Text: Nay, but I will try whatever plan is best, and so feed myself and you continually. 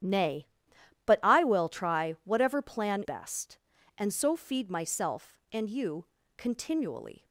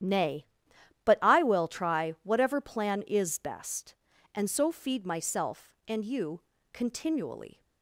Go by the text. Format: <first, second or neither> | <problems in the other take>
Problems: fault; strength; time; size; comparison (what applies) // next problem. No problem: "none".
second | starts louder than the rest; strong; until 1.6 s; 10.5 dB; strong in the second // skips "is"; at 3.0 s // pauses between "you" and "continually"; slight; at 6.0 s; 0.32 s long; slight in the second